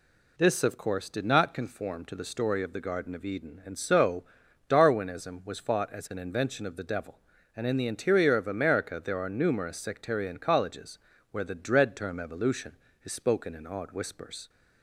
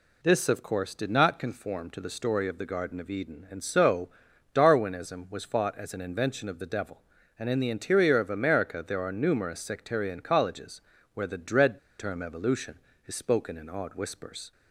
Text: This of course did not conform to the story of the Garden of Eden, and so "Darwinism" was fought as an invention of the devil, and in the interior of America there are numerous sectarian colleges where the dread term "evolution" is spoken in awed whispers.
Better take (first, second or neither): first